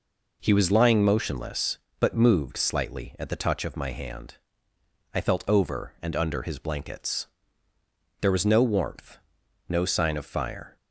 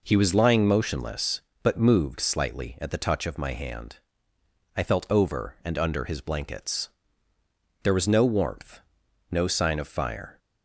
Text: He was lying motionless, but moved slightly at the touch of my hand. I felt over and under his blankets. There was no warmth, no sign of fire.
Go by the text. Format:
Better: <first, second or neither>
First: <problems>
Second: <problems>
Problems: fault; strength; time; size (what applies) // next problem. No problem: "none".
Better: neither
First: none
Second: none